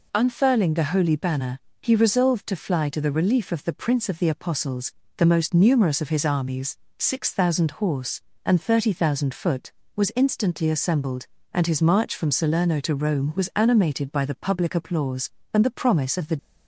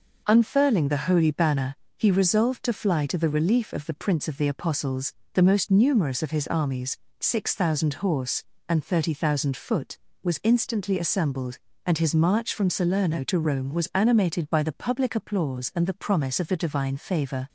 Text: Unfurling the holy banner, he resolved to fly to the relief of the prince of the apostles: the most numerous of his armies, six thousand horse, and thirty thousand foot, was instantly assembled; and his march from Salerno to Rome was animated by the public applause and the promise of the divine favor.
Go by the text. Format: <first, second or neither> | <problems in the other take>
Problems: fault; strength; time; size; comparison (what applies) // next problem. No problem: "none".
second | stops before "divine favor"; at 16.3 s